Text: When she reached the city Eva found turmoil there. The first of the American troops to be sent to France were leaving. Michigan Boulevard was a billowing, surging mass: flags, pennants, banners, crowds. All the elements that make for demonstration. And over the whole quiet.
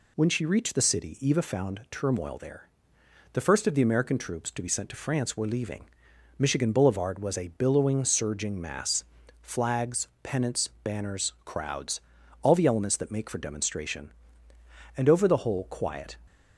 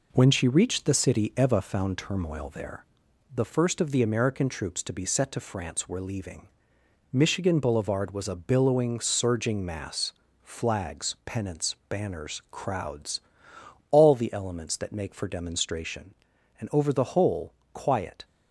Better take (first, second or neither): first